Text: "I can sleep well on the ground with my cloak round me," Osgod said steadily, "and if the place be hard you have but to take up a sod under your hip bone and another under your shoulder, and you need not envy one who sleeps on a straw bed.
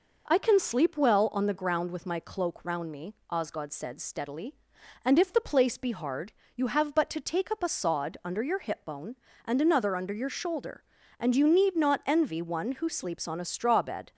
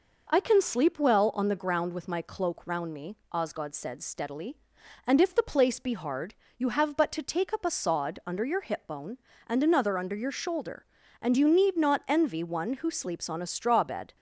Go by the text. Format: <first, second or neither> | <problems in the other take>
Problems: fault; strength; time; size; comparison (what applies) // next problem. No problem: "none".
neither | pauses between "hard" and "you"; slight; the same in both